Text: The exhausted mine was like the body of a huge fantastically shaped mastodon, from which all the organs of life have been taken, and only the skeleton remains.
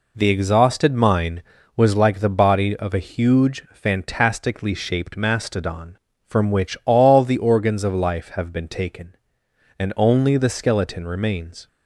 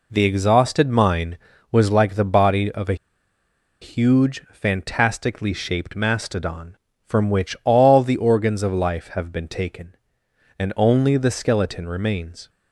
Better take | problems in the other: first | pauses between "a" and "huge"; noticeable; at 2.9 s; 0.86 s long

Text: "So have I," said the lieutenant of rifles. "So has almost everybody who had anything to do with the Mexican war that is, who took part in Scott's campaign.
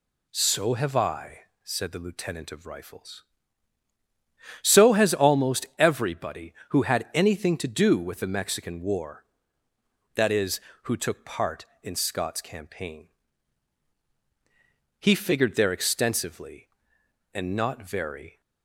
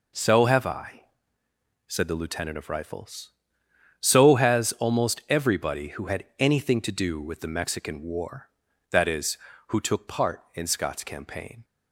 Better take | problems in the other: second | goes on to say "He figured there extensively and not very"; strong; from 14.9 s on; 3.4 s long

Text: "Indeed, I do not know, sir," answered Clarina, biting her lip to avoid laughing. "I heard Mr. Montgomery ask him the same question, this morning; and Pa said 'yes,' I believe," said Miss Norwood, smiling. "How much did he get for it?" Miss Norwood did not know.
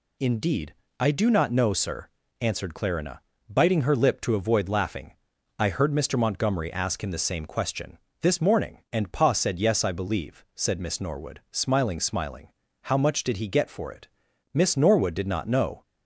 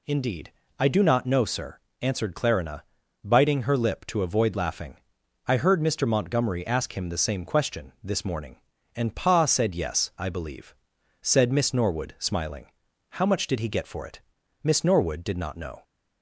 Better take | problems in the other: second | says "smiling" twice; at 11.9 s

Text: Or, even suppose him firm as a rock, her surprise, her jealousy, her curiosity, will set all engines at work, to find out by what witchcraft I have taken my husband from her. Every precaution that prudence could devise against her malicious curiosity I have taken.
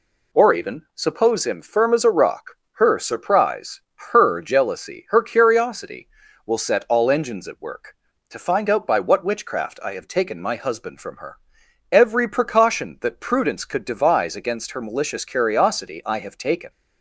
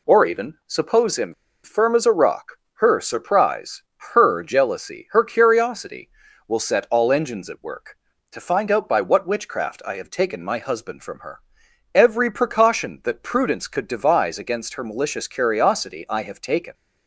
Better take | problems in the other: first | pauses between "him" and "firm"; slight; at 1.3 s; 0.30 s long

